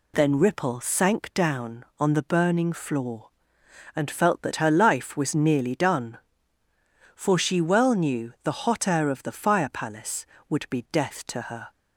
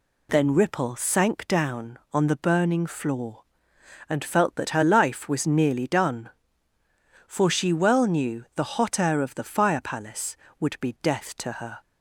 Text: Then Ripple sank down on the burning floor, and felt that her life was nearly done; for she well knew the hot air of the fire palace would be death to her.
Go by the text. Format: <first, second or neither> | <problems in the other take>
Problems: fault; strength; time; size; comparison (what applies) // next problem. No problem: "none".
neither | none